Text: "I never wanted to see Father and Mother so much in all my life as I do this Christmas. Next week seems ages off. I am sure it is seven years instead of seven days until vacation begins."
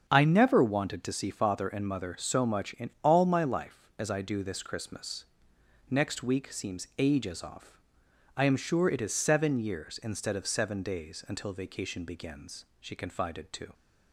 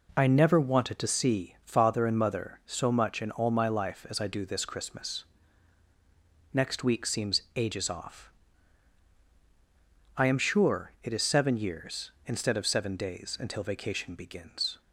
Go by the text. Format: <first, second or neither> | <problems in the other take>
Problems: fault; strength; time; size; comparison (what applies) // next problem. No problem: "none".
second | starts louder than the rest; until 1.0 s; 7 dB // goes on to say "She confided to"; noticeable; from 12.7 s on; 0.94 s long